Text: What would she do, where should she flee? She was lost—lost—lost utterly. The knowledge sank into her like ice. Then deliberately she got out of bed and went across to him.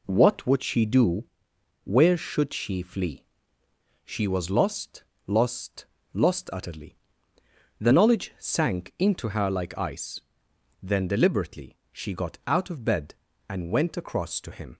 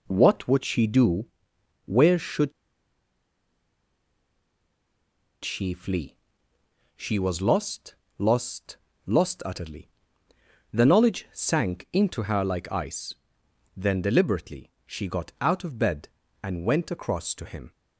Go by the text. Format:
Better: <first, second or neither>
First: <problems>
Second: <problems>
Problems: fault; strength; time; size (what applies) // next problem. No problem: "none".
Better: first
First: pauses between "deliberately" and "she"; slight; at 11.7 s; 0.16 s long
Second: pauses between "should" and "she"; strong; at 2.5 s; 2.9 s long // pauses between "deliberately" and "she"; slight; at 14.7 s; 0.16 s long